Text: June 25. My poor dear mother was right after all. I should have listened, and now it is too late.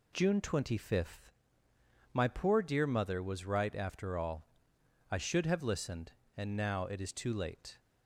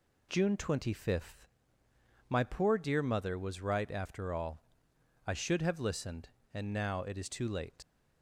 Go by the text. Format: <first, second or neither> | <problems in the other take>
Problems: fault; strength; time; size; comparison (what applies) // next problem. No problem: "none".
first | leaves "late" unfinished; at 7.8 s; 115 ms